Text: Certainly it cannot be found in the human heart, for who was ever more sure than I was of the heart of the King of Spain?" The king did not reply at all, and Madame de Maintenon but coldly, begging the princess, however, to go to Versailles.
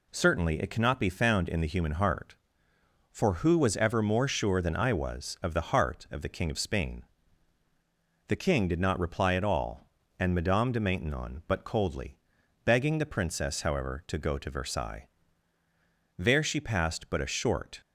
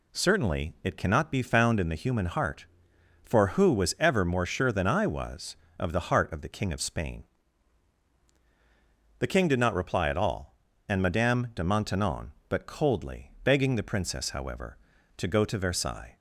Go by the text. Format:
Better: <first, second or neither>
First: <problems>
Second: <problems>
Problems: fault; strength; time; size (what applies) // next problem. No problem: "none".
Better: second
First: goes on to say "There she passed but a short"; from 16.1 s on; 1.6 s long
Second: none